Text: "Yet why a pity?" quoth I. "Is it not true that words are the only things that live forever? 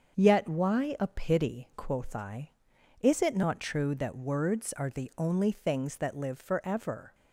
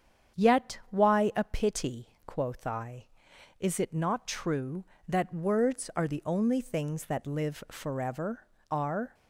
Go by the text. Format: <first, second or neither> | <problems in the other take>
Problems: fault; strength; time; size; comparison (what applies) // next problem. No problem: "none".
first | starts louder than the rest; strong; until 1.5 s; 8 dB; also in the first // goes on to say "Are"; slight; from 8.6 s on; 0.46 s long